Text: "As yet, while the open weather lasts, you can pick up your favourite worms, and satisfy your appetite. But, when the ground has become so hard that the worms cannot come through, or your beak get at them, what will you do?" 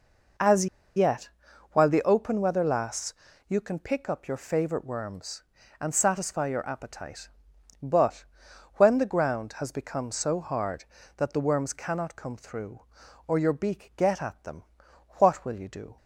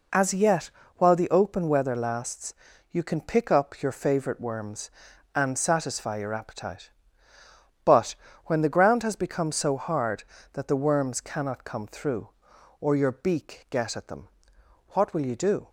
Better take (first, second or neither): second